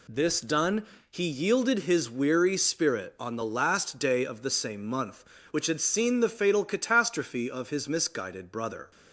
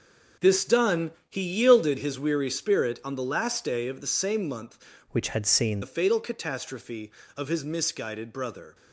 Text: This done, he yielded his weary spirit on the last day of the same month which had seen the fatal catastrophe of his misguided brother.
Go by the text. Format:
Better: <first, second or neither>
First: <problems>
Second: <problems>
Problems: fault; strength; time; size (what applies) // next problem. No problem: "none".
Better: first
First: none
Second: changes voice from "which" to "seen"; from 5.1 to 5.8 s; 0.7 s long